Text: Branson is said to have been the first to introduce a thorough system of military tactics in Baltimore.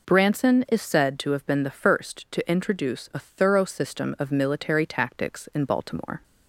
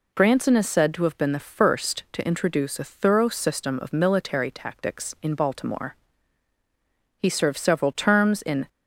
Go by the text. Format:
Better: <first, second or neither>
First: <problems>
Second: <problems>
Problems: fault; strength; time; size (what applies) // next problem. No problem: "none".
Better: first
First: none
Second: goes on to say "He served several terms in"; from 7.1 s on; 1.5 s long